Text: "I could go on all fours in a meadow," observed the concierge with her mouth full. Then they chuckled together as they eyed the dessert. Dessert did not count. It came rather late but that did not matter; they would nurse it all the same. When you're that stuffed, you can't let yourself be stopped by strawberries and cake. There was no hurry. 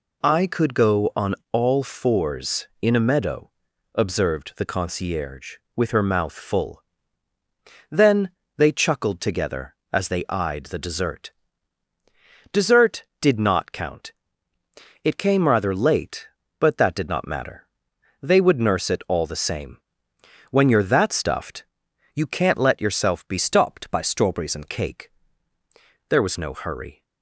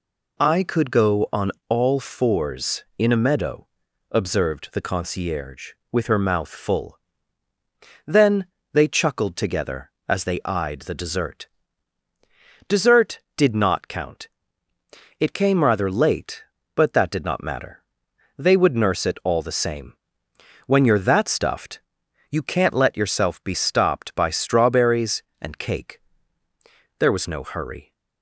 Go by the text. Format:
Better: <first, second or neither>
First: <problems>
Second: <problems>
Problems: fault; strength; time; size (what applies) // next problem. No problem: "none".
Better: second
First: pauses between "on" and "all"; slight; at 1.3 s; 0.16 s long // pauses between "Then" and "they"; slight; at 8.3 s; 0.26 s long // changes voice from "stopped" to "and"; from 23.3 to 24.6 s; 1.3 s long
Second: pauses between "on" and "all"; slight; at 1.5 s; 0.16 s long // pauses between "Then" and "they"; slight; at 8.4 s; 0.26 s long